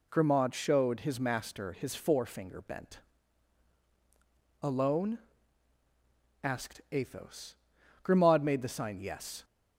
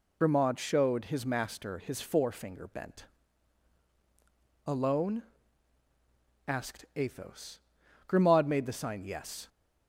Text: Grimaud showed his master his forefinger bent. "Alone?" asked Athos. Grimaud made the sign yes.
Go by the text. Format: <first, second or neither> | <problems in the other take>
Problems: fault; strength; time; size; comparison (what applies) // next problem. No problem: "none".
first | loses the start of "Grimaud"; at 0.2 s; 65 ms